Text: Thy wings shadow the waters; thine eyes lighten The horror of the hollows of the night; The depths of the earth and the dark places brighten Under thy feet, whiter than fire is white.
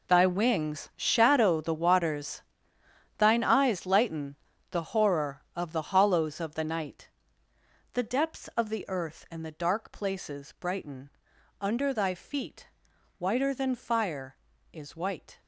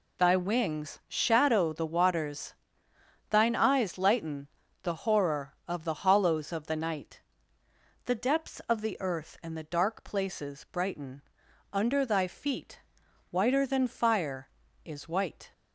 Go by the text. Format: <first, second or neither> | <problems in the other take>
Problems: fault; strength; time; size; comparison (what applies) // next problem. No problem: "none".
second | gets quieter; strong; throughout; 15 dB // pauses between "lighten" and "The"; slight; at 4.3 s; 0.36 s long; slight in the second // pauses between "brighten" and "Under"; noticeable; at 11.1 s; 0.50 s long; noticeable in the second